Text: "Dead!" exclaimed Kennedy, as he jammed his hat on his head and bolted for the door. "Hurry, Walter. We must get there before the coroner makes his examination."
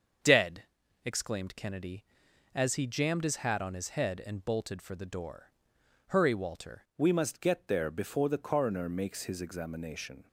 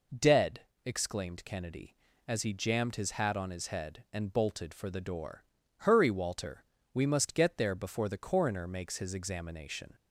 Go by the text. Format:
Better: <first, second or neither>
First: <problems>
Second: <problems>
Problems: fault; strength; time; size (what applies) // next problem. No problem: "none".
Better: second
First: starts louder than the rest; until 1.6 s; 7 dB // changes voice at "We"; from 6.9 s on; 3.3 s long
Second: none